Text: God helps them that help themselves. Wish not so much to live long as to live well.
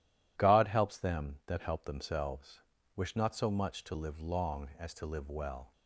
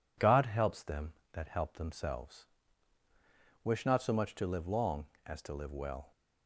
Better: neither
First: none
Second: none

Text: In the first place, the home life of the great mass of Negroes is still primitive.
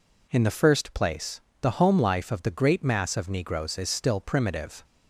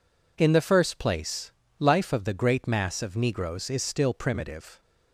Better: first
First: none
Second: skips "the home"; at 1.6 s

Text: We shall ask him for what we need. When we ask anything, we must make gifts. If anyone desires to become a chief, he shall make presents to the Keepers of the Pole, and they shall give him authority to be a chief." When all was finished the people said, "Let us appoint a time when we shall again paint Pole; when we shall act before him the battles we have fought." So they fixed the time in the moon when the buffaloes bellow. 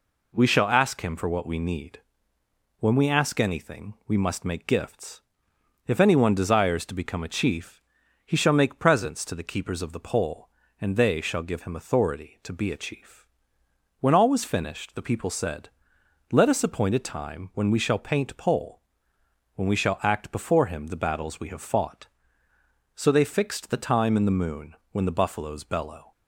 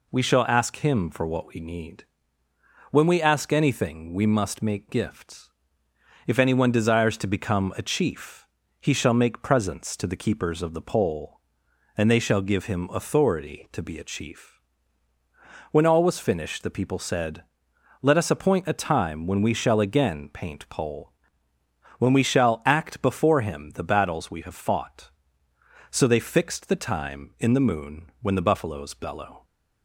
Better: second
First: skips "again"; at 18.0 s // pauses between "moon" and "when"; slight; at 24.7 s; 0.16 s long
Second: none

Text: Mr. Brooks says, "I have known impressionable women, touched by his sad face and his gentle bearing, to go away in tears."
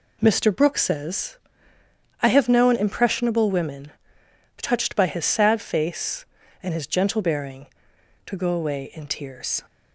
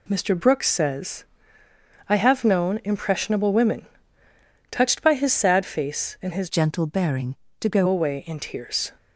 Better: first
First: none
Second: changes voice from "gentle" to "go"; from 6.4 to 7.8 s; 1.4 s long

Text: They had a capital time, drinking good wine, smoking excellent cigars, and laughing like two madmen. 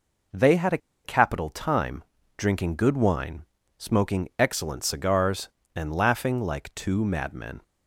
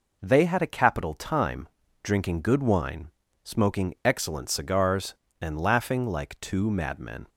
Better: second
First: pauses between "a" and "capital"; slight; at 0.7 s; 0.26 s long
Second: none

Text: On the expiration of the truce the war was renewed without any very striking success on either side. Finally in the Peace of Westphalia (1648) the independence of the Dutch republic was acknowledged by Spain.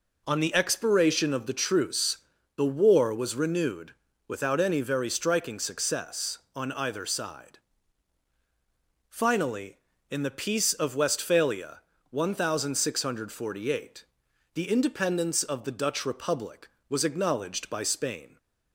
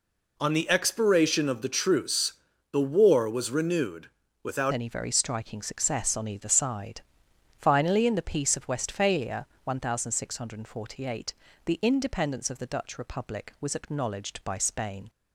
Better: first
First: pauses between "truce" and "the"; at 2.1 s; 0.38 s long // pauses between "renewed" and "without"; slight; at 3.9 s; 0.34 s long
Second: pauses between "truce" and "the"; at 2.3 s; 0.38 s long // pauses between "renewed" and "without"; slight; at 4.0 s; 0.34 s long // changes voice at "any"; from 4.7 s on; 10.3 s long

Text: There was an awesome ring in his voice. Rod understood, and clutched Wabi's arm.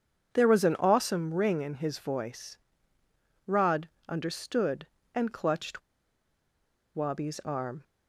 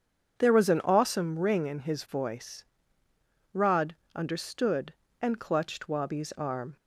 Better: second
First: starts louder than the rest; strong; until 1.3 s; 7.5 dB // pauses between "Rod" and "understood"; slight; at 3.8 s; 0.18 s long // pauses between "clutched" and "Wabi's"; at 5.8 s; 1.1 s long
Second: pauses between "Rod" and "understood"; slight; at 3.9 s; 0.18 s long

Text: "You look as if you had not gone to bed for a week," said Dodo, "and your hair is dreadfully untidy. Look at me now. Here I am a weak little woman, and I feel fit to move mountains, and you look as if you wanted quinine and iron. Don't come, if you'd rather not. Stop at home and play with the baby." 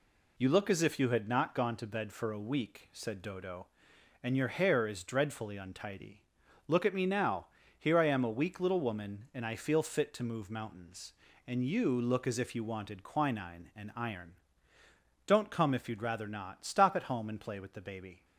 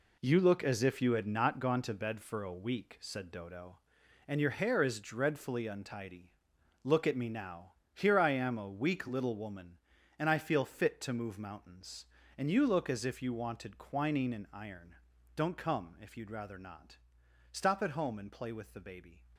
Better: first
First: none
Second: gets quieter; strong; throughout; 9 dB

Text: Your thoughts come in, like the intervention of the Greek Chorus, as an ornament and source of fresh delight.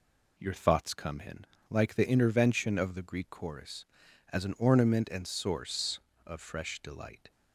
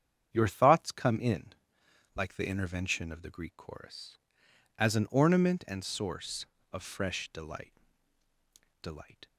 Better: first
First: none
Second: starts louder than the rest; strong; until 1.3 s; 8 dB // says "delight" twice; at 8.8 s

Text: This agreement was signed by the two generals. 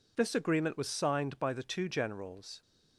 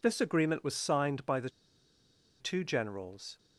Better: first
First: none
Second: pauses between "the" and "two"; noticeable; at 1.4 s; 0.91 s long

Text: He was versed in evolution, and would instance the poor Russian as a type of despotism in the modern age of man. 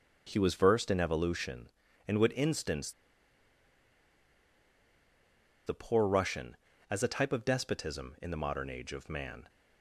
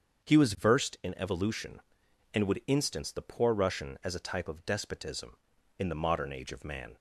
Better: second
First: starts louder than the rest; until 1.2 s; 6.5 dB // pauses between "instance" and "the"; strong; at 2.9 s; 2.7 s long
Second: starts louder than the rest; strong; until 1.4 s; 7 dB

